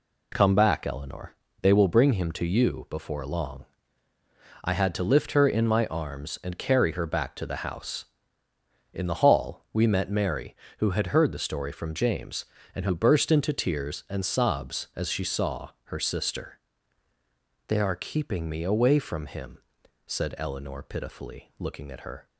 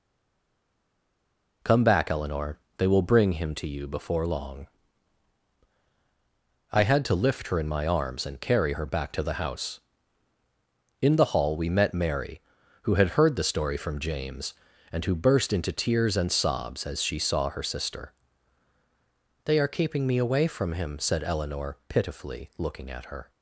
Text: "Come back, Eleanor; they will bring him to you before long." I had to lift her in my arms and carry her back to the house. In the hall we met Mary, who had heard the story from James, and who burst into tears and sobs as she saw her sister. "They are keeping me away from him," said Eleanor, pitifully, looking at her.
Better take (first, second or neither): first